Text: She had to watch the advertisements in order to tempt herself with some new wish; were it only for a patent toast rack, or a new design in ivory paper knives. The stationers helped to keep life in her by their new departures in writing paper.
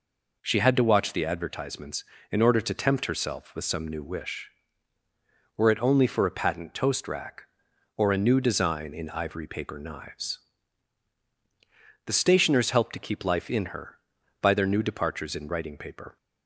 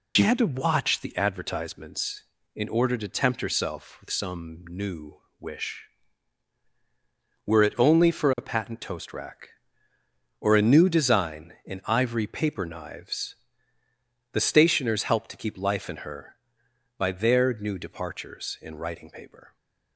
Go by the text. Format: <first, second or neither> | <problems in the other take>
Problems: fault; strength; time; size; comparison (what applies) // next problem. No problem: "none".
first | loses the start of "She"; at 0.1 s; 70 ms // pauses between "new" and "wish"; slight; at 5.1 s; 0.22 s long